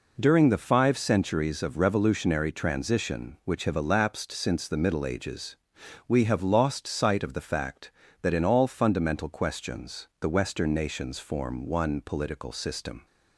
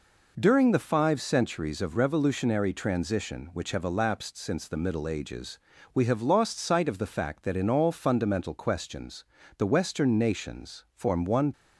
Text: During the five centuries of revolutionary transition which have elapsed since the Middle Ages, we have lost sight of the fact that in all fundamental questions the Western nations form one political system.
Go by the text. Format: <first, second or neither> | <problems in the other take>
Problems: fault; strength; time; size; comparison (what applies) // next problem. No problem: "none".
first | pauses between "questions" and "the"; slight; at 9.2 s; 0.32 s long // stops before "political system"; at 11.5 s